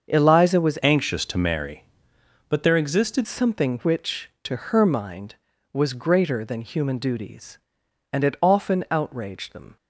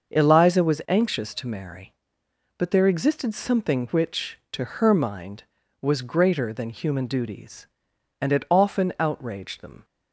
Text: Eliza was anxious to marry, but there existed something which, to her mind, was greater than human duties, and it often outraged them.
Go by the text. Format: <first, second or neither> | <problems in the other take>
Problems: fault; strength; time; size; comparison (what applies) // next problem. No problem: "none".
second | starts louder than the rest; until 1.1 s; 6.5 dB; also in the second // changes voice from "anxious" to "existed"; from 0.8 to 3.2 s; 2.4 s long